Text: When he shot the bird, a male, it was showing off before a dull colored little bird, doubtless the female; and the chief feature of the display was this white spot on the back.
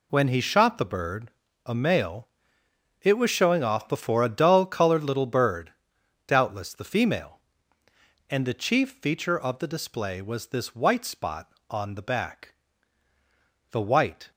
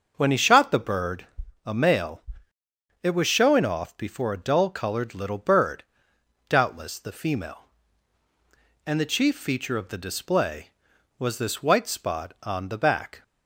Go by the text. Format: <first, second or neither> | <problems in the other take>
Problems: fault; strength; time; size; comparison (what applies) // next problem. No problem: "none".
second | goes on to say "The white"; from 13.7 s on; 0.60 s long